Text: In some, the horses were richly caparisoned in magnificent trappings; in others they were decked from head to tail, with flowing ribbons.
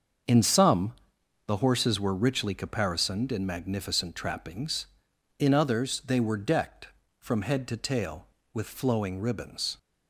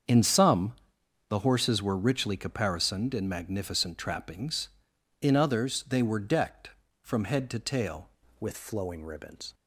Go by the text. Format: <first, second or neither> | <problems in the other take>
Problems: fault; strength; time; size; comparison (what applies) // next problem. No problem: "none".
first | starts louder than the rest; strong; until 1.6 s; 7 dB; also in the first // changes voice at "with"; from 8.3 s on; 1.2 s long